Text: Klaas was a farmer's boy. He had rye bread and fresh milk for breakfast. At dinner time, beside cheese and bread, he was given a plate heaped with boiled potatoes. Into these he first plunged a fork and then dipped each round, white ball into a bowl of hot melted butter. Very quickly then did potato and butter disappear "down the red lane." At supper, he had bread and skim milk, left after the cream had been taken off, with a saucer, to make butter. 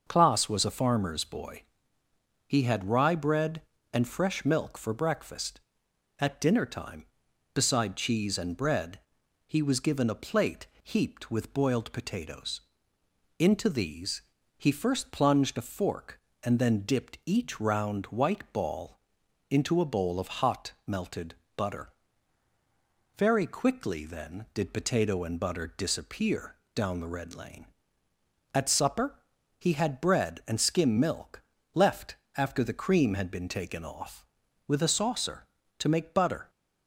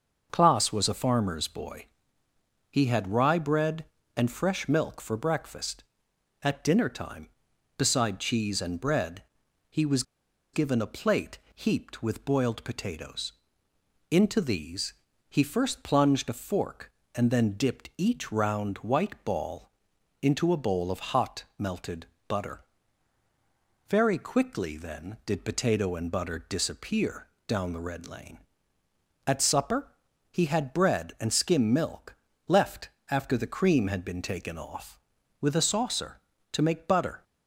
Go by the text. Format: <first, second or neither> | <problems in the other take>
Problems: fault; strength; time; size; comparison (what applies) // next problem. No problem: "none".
first | starts louder than the rest; until 1.3 s; 6 dB; also in the first // pauses between "was" and "given"; noticeable; at 10.0 s; 0.50 s long // pauses between "plate" and "heaped"; slight; at 11.3 s; 0.16 s long; slight in the first // pauses between "these" and "he"; slight; at 14.9 s; 0.36 s long; slight in the first // pauses between "ball" and "into"; noticeable; at 19.6 s; 0.52 s long; noticeable in the first // pauses between "melted" and "butter"; slight; at 22.0 s; 0.22 s long; slight in the first // pauses between "disappear" and "down"; slight; at 27.2 s; 0.20 s long; slight in the first // pauses between "left" and "after"; slight; at 32.8 s; 0.22 s long; slight in the first